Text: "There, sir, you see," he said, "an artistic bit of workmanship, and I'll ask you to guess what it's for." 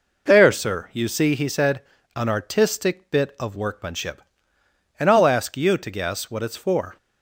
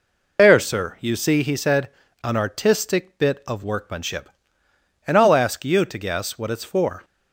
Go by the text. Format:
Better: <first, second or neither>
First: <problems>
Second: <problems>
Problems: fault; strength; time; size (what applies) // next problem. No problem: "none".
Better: first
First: none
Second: loses the start of "There"; at 0.3 s; 65 ms